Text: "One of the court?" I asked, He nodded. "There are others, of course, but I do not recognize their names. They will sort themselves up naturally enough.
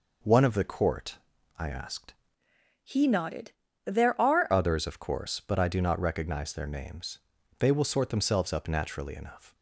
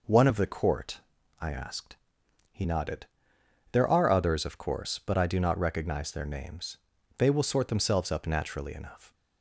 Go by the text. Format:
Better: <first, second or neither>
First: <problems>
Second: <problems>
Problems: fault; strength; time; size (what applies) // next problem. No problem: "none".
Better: second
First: changes voice from "He" to "are"; from 2.8 to 4.4 s; 1.6 s long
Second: none